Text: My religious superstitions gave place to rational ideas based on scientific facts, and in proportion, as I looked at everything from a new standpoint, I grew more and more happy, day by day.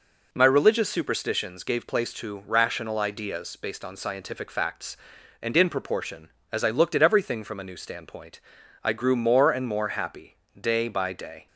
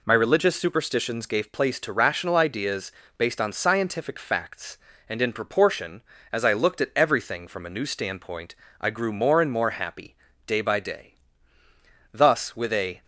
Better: first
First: none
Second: pauses between "ideas" and "based"; slight; at 2.9 s; 0.26 s long // goes on to say "Thus with a"; noticeable; from 12.1 s on; 0.92 s long

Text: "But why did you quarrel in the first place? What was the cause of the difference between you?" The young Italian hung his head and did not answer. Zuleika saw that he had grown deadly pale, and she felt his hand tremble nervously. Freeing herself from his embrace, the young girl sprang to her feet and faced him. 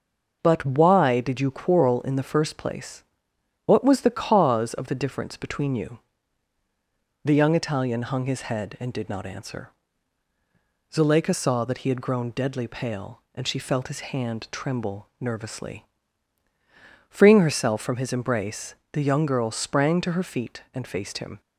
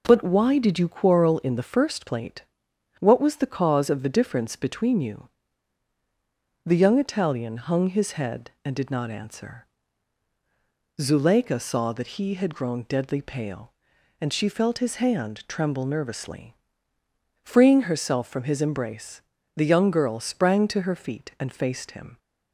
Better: first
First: none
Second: says "plate" for "place"; at 2.0 s

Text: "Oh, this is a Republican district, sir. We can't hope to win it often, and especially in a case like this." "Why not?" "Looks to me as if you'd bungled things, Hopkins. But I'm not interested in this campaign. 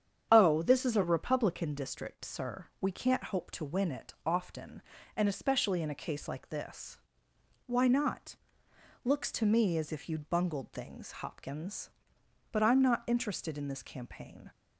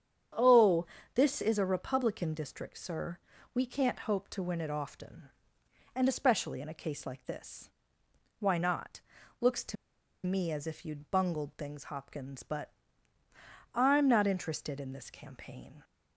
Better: first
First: starts louder than the rest; strong; until 1.3 s; 8.5 dB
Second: starts louder than the rest; strong; until 1.6 s; 8 dB // pauses between "to" and "me"; noticeable; at 9.7 s; 0.50 s long // pauses between "But" and "I'm"; at 12.7 s; 1.0 s long

